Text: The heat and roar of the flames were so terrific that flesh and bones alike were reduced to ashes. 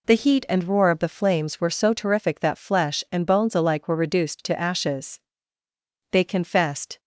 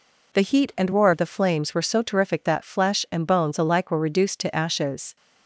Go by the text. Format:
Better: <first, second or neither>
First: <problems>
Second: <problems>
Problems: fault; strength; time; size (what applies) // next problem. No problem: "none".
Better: second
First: goes on to say "They confessed"; noticeable; from 6.1 s on; 0.88 s long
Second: none